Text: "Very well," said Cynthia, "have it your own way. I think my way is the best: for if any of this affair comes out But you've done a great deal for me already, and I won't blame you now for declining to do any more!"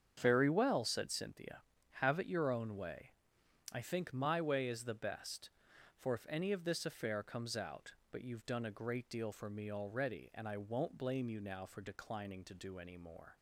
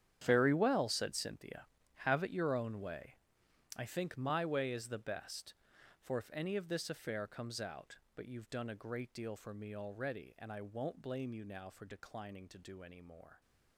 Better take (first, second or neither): first